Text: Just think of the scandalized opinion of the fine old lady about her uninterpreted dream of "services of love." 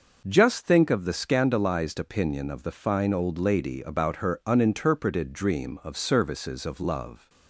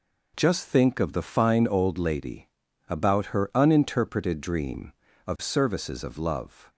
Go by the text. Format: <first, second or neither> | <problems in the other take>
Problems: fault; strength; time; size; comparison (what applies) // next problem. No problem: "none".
first | skips "the scandalized opinion of"; at 1.1 s // pauses between "lady" and "about"; at 2.4 s; 0.40 s long